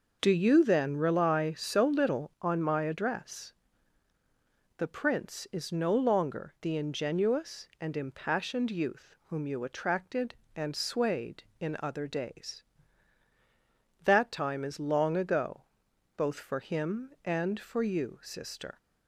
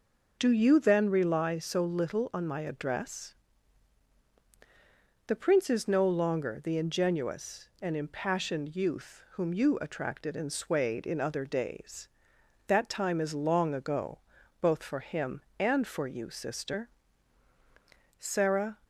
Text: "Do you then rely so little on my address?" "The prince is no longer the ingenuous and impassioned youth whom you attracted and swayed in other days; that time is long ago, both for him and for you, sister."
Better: first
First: none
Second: goes on to say "Sarah"; from 18.1 s on; 0.58 s long

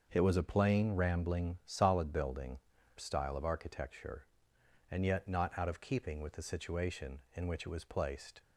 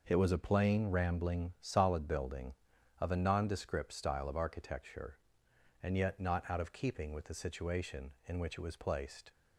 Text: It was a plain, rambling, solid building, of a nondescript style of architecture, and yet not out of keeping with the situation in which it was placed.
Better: second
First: starts louder than the rest; until 1.1 s; 6.5 dB // skips "of a nondescript"; at 2.7 s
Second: none

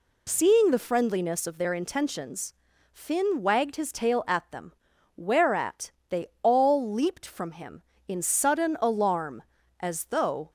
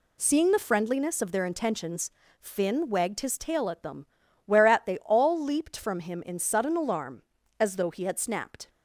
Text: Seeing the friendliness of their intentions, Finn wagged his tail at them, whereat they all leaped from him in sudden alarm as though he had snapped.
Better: second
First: pauses between "whereat" and "they"; slight; at 5.8 s; 0.20 s long // pauses between "they" and "all"; slight; at 6.2 s; 0.16 s long // stops before "he had snapped"; at 10.4 s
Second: none

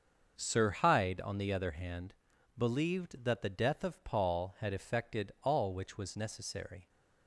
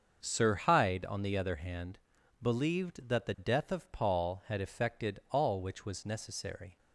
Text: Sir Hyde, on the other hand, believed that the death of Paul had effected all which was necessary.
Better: neither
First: starts louder than the rest; until 1.3 s; 6.5 dB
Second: starts louder than the rest; until 1.2 s; 6.5 dB

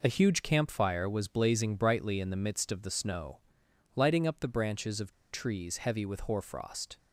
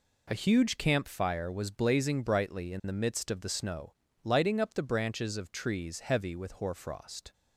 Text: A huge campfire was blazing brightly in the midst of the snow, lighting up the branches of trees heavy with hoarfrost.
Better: second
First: pauses between "of" and "trees"; slight; at 5.1 s; 0.18 s long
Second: none

